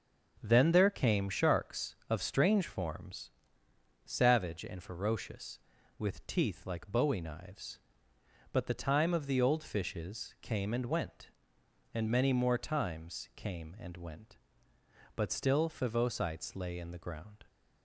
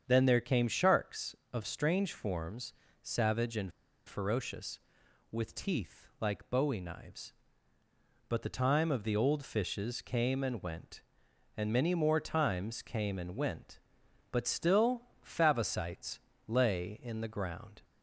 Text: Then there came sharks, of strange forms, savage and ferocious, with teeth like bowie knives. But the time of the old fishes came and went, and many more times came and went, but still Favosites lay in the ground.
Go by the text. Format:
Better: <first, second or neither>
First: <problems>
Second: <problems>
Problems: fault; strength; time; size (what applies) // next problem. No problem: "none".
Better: first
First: starts louder than the rest; noticeable; until 1.4 s; 6 dB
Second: starts louder than the rest; strong; until 1.0 s; 7.5 dB // pauses between "and" and "ferocious"; at 3.7 s; 0.36 s long // pauses between "still" and "Favosites"; slight; at 15.0 s; 0.20 s long // pauses between "Favosites" and "lay"; slight; at 16.1 s; 0.28 s long